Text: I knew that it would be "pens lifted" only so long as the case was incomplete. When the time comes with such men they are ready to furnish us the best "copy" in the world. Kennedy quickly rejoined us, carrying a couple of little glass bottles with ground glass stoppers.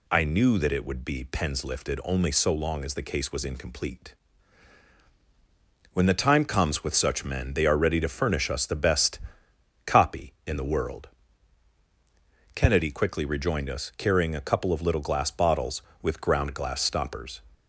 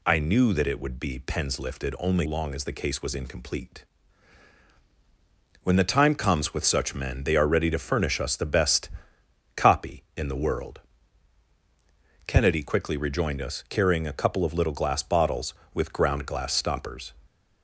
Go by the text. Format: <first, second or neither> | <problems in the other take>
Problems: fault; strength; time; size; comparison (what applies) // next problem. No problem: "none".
first | skips "so"; at 2.2 s // pauses between "best" and "copy"; noticeable; at 8.8 s; 0.66 s long; noticeable in the first